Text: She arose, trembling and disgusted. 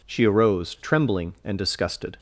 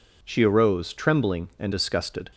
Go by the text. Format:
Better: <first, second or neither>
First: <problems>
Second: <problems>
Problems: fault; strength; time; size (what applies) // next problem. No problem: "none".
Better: neither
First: none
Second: none